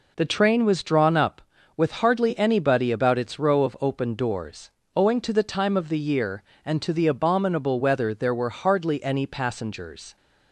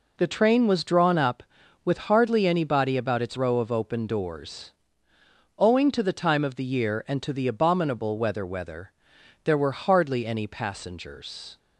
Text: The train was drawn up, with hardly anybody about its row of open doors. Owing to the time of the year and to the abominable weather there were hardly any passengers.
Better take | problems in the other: first | says "weather" twice; at 8.4 s

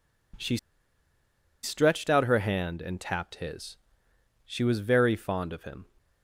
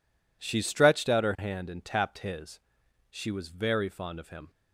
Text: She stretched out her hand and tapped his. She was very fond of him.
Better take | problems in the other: second | pauses between "She" and "stretched"; at 0.5 s; 1.0 s long

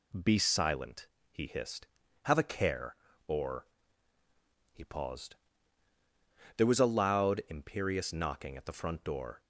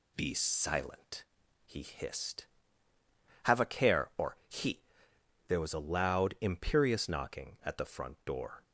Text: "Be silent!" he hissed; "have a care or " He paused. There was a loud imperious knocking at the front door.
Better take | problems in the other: first | skips "paused"; at 5.1 s

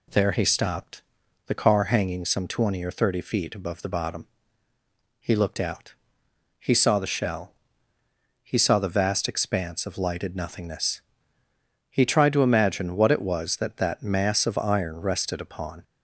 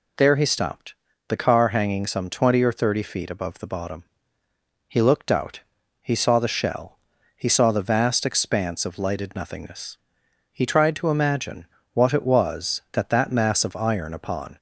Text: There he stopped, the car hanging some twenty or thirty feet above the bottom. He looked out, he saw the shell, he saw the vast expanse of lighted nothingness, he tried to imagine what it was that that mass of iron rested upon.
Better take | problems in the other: first | pauses between "imagine" and "what"; slight; at 11.6 s; 0.28 s long // skips "rested"; at 14.1 s

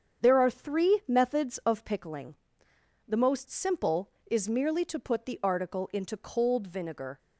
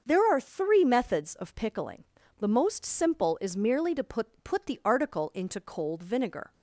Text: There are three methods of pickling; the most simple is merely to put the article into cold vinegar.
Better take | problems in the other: first | starts louder than the rest; until 1.0 s; 6.5 dB; strong in the first // says "put" twice; at 4.4 s

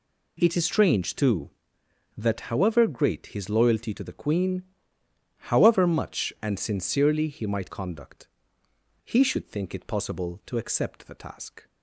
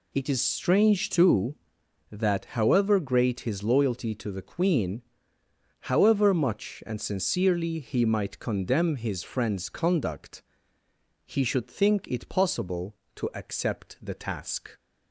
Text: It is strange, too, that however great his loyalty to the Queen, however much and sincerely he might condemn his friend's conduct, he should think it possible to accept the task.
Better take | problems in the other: second | skips "condemn his friend's"; at 7.7 s

